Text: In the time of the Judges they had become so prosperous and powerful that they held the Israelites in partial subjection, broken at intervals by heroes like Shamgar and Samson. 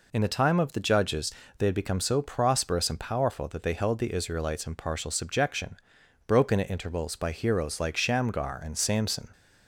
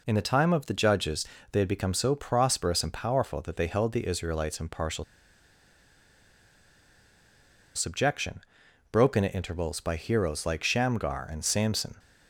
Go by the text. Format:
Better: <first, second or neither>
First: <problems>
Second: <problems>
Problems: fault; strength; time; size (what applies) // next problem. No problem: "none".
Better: first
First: pauses between "Judges" and "they"; slight; at 1.3 s; 0.26 s long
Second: pauses between "Judges" and "they"; slight; at 1.2 s; 0.26 s long // pauses between "partial" and "subjection"; strong; at 5.0 s; 2.7 s long